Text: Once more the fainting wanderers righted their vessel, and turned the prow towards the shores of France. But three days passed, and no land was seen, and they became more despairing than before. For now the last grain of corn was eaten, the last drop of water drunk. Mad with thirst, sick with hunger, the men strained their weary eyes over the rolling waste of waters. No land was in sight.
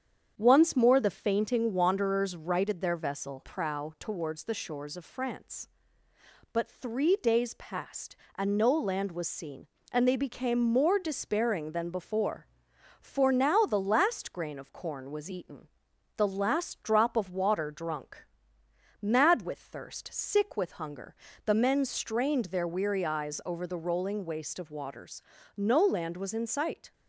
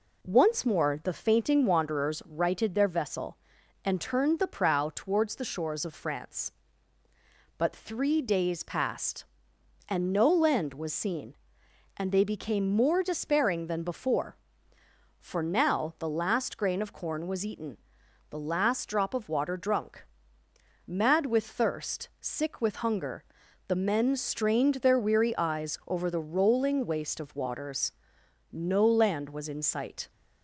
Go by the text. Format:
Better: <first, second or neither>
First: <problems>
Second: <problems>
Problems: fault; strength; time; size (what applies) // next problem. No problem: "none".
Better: second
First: starts louder than the rest; strong; until 1.3 s; 8 dB // skips "and turned the"; at 3.4 s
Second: none